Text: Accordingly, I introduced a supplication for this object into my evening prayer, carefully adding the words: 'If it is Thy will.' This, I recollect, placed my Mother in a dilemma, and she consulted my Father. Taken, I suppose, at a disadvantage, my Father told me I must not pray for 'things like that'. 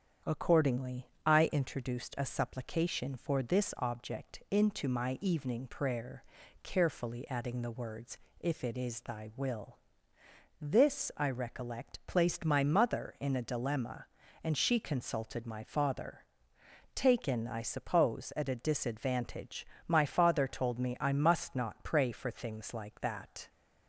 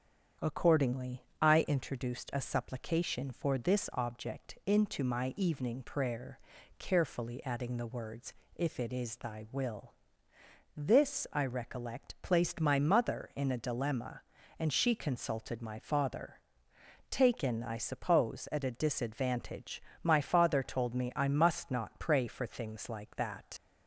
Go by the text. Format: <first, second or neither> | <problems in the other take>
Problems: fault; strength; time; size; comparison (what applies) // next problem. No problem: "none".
first | starts louder than the rest; strong; until 1.5 s; 8 dB; strong in the first // leaves "that" unfinished; at 23.5 s; 75 ms